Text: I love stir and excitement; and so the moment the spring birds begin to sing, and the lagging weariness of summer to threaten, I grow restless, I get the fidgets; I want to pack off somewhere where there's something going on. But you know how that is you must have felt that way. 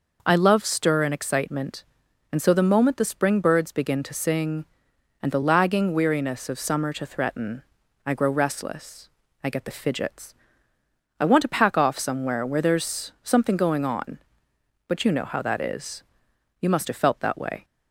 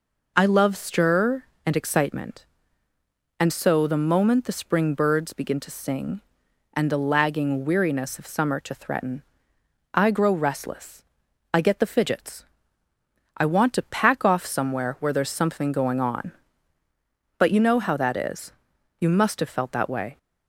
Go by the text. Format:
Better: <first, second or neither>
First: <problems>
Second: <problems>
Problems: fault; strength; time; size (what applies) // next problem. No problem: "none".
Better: neither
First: pauses between "is" and "you"; noticeable; at 16.0 s; 0.58 s long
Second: pauses between "is" and "you"; noticeable; at 18.5 s; 0.48 s long